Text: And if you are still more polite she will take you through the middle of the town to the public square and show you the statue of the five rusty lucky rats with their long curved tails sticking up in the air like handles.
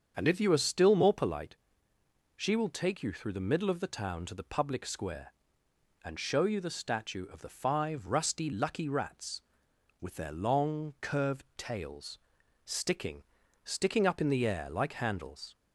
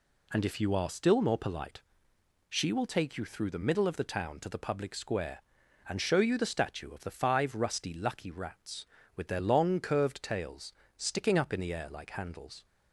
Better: second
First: starts louder than the rest; strong; until 1.1 s; 7 dB // pauses between "polite" and "she"; noticeable; at 1.5 s; 0.80 s long // pauses between "tails" and "sticking"; noticeable; at 12.1 s; 0.46 s long // says "sticking" twice; at 13.6 s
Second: pauses between "polite" and "she"; noticeable; at 1.8 s; 0.68 s long // pauses between "tails" and "sticking"; slight; at 10.7 s; 0.24 s long

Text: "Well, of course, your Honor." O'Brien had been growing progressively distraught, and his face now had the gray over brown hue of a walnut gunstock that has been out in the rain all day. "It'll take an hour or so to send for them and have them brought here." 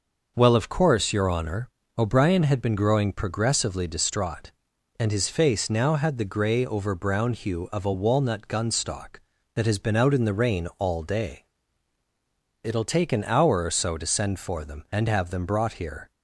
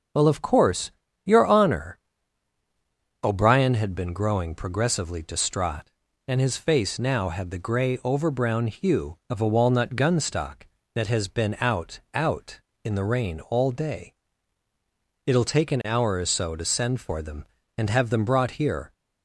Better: first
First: starts louder than the rest; noticeable; until 1.3 s; 6 dB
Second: starts louder than the rest; until 1.4 s; 6 dB // says "out" twice; at 12.1 s

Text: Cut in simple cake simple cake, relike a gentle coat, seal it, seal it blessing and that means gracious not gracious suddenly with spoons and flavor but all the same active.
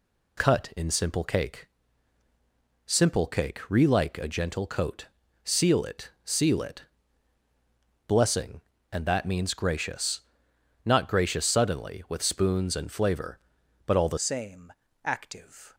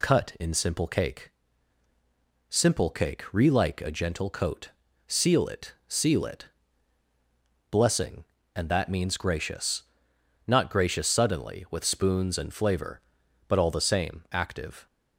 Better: second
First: pauses between "cake" and "simple"; at 1.6 s; 1.2 s long // pauses between "it" and "blessing"; at 6.8 s; 1.2 s long // pauses between "gracious" and "not"; noticeable; at 10.2 s; 0.64 s long // changes voice at "same"; from 14.1 s on; 1.6 s long // pauses between "same" and "active"; slight; at 14.7 s; 0.32 s long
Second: pauses between "cake" and "simple"; at 1.2 s; 1.2 s long // pauses between "it" and "blessing"; at 6.4 s; 1.2 s long // pauses between "gracious" and "not"; noticeable; at 9.8 s; 0.64 s long

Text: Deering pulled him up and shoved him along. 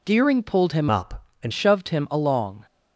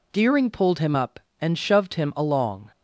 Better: second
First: changes voice from "up" to "and"; from 0.9 to 1.5 s; 0.6 s long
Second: none

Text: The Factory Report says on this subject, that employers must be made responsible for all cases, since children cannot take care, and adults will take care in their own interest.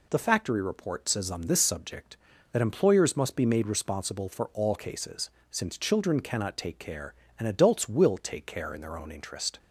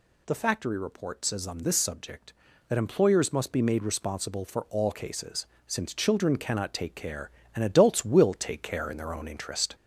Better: first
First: none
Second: gets louder; slight; throughout; 3 dB

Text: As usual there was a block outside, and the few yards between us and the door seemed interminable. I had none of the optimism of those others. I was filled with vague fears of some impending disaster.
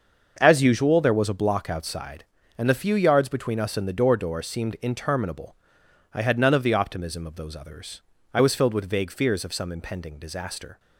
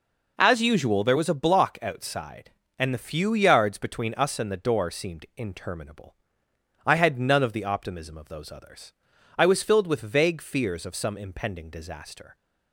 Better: second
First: starts louder than the rest; until 1.4 s; 6.5 dB // says "door" twice; at 4.1 s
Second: none

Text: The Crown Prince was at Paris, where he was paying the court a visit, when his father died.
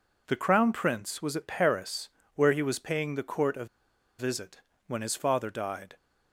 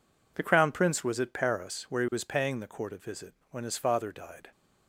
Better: second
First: pauses between "a" and "visit"; noticeable; at 3.6 s; 0.53 s long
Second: none

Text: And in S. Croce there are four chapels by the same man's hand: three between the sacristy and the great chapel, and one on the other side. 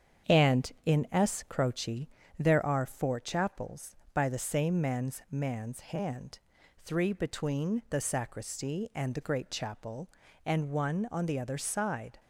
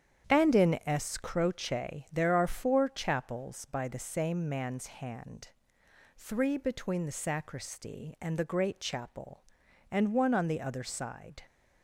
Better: second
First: starts louder than the rest; strong; until 1.4 s; 7.5 dB // pauses between "Croce" and "there"; slight; at 2.0 s; 0.30 s long // says "man's" twice; at 5.2 s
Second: starts louder than the rest; strong; until 1.3 s; 9 dB

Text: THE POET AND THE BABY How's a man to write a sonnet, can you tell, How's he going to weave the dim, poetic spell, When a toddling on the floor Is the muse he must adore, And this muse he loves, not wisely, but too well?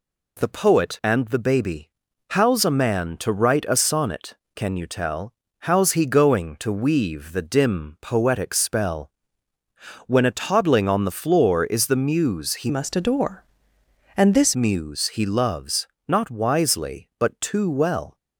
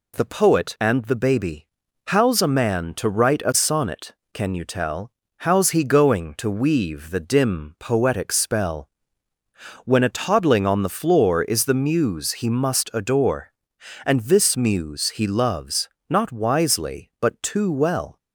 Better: second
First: pauses between "BABY" and "How's"; at 1.8 s; 0.40 s long // changes voice from "must" to "this"; from 12.6 to 14.5 s; 1.9 s long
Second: pauses between "BABY" and "How's"; at 1.6 s; 0.40 s long

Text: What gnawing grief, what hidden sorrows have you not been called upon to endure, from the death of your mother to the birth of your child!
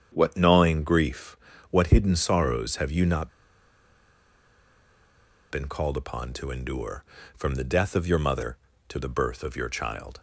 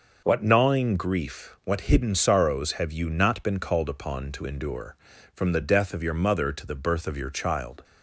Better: second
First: starts louder than the rest; strong; until 1.1 s; 8 dB // pauses between "not" and "been"; strong; at 3.2 s; 2.2 s long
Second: none

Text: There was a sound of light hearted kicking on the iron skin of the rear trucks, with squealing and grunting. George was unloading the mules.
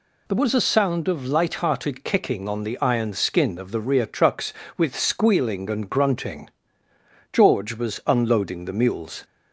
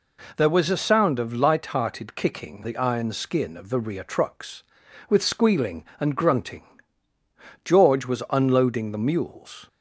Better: first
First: none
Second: skips "on"; at 2.6 s

